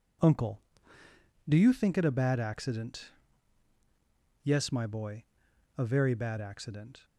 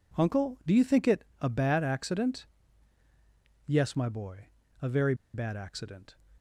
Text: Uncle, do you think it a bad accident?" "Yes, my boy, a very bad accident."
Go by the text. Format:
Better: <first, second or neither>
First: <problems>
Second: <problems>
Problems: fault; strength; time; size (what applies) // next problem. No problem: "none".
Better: first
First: none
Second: pauses between "it" and "a"; slight; at 1.2 s; 0.16 s long // pauses between "very" and "bad"; slight; at 5.1 s; 0.19 s long